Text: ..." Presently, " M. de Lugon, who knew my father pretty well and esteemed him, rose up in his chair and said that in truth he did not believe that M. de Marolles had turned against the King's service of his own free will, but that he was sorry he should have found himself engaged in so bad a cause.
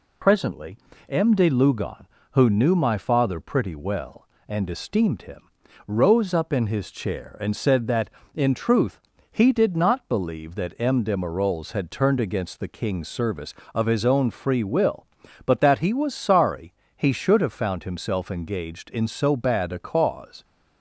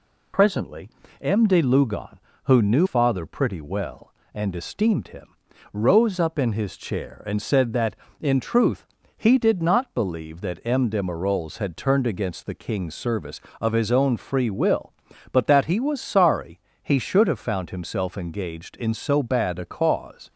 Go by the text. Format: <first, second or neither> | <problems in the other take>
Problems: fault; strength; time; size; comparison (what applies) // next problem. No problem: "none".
first | skips "my"; at 2.8 s // pauses between "truth" and "he"; slight; at 8.8 s; 0.32 s long; slight in the first // pauses between "sorry" and "he"; slight; at 16.5 s; 0.24 s long; slight in the first